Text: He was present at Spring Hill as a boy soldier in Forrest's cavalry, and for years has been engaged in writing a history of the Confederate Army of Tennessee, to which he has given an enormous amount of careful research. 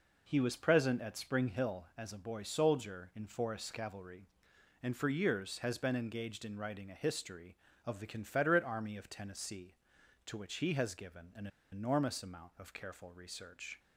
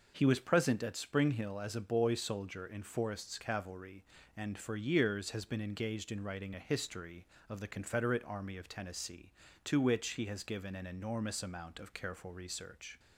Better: second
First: pauses between "an" and "enormous"; slight; at 11.4 s; 0.24 s long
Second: none

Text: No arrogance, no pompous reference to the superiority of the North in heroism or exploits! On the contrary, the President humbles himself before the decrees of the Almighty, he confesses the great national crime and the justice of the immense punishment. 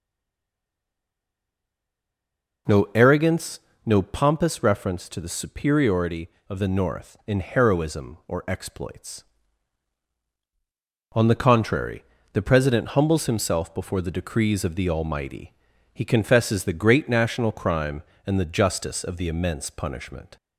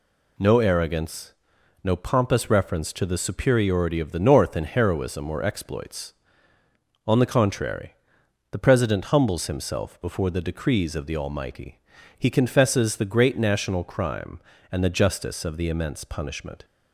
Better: second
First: stays silent before the first word; strong; until 2.6 s; 2.6 s long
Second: none

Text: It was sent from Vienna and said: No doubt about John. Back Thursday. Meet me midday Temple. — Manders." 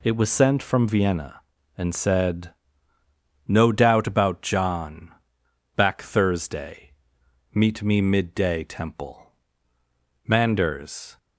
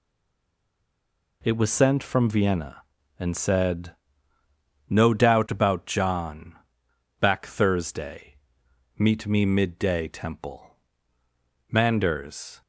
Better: first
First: none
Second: stays silent before the first word; noticeable; until 1.4 s; 1.4 s long

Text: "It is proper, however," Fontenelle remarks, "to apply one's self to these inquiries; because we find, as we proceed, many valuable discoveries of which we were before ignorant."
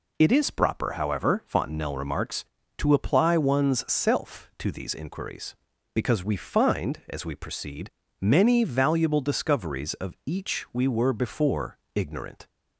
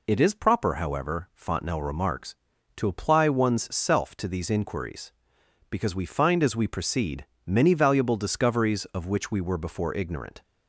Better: second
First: says "each" for "which"; at 10.2 s // pauses between "before" and "ignorant"; slight; at 11.7 s; 0.18 s long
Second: none

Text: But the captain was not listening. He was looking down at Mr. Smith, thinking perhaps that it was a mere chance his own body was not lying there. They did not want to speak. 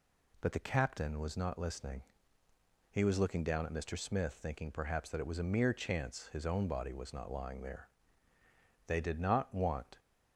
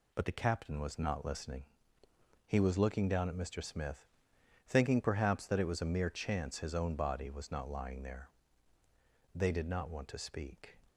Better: second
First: stops before "to speak"; at 9.9 s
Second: none

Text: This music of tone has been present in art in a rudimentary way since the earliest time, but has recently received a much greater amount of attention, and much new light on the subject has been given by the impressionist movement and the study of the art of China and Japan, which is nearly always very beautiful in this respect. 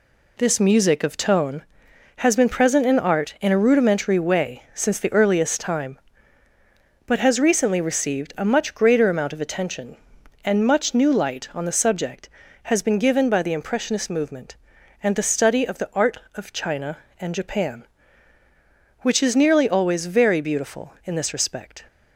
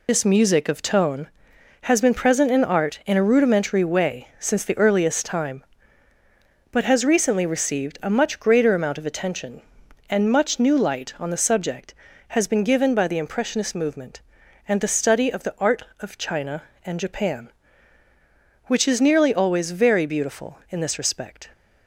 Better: first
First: none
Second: loses the start of "This"; at 0.0 s; 50 ms

